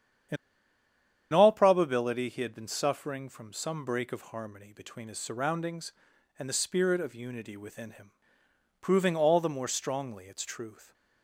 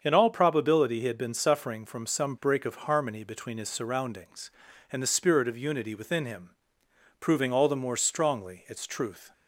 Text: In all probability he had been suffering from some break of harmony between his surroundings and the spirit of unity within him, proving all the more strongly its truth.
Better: second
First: starts louder than the rest; strong; until 2.2 s; 9 dB // pauses between "In" and "all"; noticeable; at 0.3 s; 0.96 s long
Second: starts louder than the rest; until 1.0 s; 7 dB

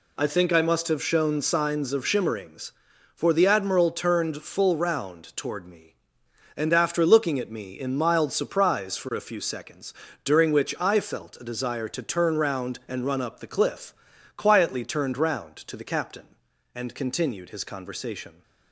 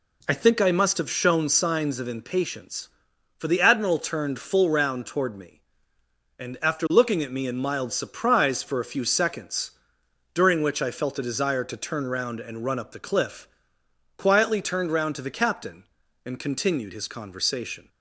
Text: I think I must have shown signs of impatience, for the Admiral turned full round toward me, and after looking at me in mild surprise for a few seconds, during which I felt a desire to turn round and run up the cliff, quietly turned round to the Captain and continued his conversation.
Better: second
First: says "shimmerings" for "impatience"; at 2.0 s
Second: none

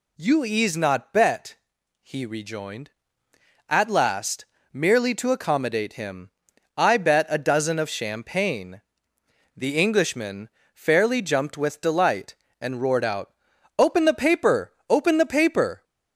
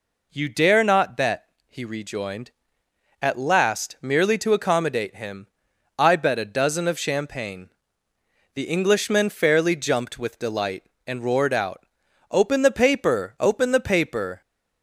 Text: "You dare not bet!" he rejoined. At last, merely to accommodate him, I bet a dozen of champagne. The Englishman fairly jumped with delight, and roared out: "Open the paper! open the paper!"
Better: second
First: says "ease" for "dare"; at 0.4 s // pauses between "Englishman" and "fairly"; slight; at 10.4 s; 0.26 s long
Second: none

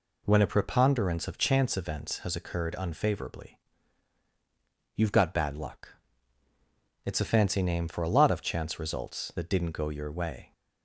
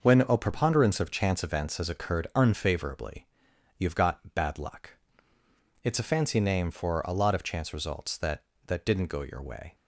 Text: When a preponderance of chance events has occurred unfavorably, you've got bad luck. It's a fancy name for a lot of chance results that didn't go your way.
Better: first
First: none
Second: starts louder than the rest; noticeable; until 1.0 s; 6 dB // says "that" twice; at 8.6 s

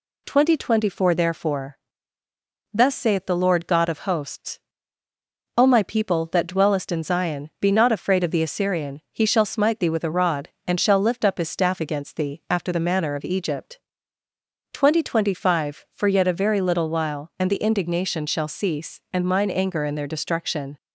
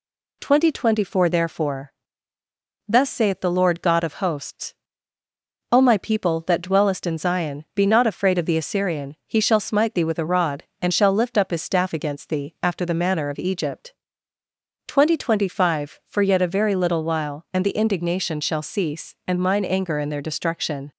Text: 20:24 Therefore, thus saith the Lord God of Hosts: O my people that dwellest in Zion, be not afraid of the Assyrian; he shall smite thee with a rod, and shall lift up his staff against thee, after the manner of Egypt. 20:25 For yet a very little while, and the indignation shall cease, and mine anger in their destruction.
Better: neither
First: none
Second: none

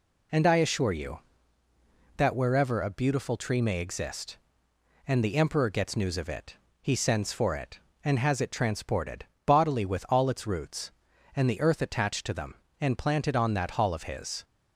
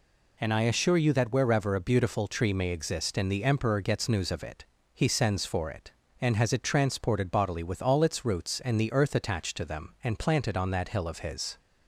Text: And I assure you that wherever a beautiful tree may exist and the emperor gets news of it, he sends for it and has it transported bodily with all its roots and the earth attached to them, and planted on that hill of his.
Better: second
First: pauses between "transported" and "bodily"; slight; at 9.2 s; 0.20 s long // says "hall" for "hill"; at 13.7 s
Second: none

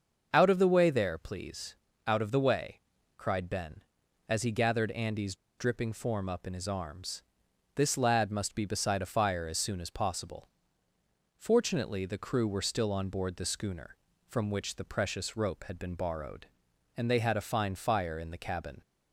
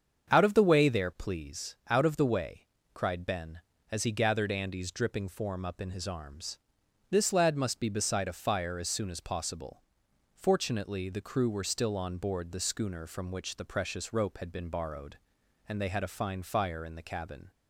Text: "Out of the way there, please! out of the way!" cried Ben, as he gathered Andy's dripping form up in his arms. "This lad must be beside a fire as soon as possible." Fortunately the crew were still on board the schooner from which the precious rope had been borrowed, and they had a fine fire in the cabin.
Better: second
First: starts louder than the rest; until 1.3 s; 6.5 dB // pauses between "Andy's" and "dripping"; slight; at 5.3 s; 0.23 s long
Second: starts louder than the rest; strong; until 1.3 s; 7.5 dB

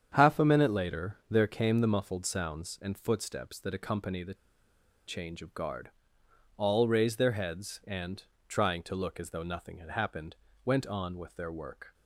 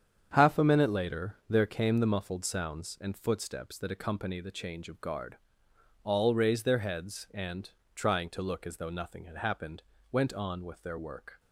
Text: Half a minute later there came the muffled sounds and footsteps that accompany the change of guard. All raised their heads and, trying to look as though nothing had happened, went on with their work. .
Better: second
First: starts louder than the rest; strong; until 1.1 s; 8 dB // pauses between "the" and "change"; noticeable; at 4.3 s; 0.72 s long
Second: starts louder than the rest; strong; until 1.3 s; 8 dB

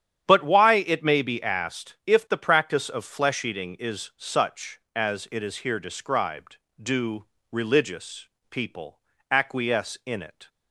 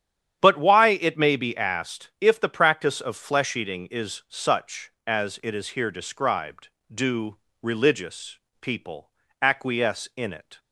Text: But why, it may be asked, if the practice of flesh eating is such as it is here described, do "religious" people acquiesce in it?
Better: neither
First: starts louder than the rest; strong; until 1.2 s; 9.5 dB // pauses between "do" and "religious"; slight; at 7.2 s; 0.26 s long // pauses between "religious" and "people"; slight; at 8.2 s; 0.22 s long // pauses between "people" and "acquiesce"; slight; at 8.9 s; 0.32 s long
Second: starts louder than the rest; strong; until 1.4 s; 9.5 dB // pauses between "do" and "religious"; slight; at 7.3 s; 0.25 s long // pauses between "religious" and "people"; slight; at 8.3 s; 0.22 s long // pauses between "people" and "acquiesce"; slight; at 9.0 s; 0.32 s long

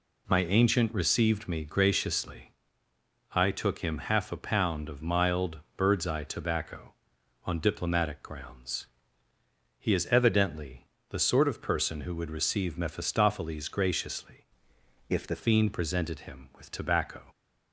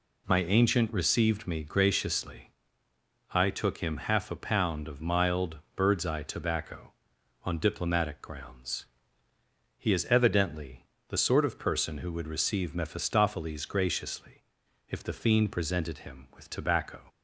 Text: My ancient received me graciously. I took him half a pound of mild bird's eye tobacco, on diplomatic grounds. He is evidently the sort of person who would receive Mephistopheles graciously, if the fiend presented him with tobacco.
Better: second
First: pauses between "mild" and "bird's"; slight; at 5.5 s; 0.16 s long // pauses between "evidently" and "the"; slight; at 10.8 s; 0.22 s long // changes voice from "if" to "the"; from 15.0 to 15.3 s; 0.3 s long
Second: pauses between "mild" and "bird's"; slight; at 5.5 s; 0.16 s long // pauses between "evidently" and "the"; slight; at 10.8 s; 0.22 s long

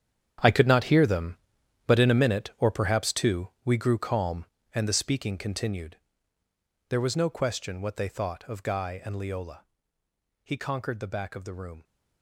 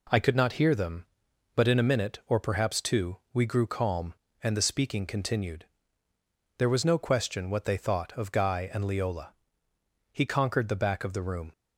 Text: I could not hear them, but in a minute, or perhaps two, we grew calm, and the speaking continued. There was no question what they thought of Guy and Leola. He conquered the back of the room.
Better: second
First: gets quieter; strong; throughout; 14.5 dB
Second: none

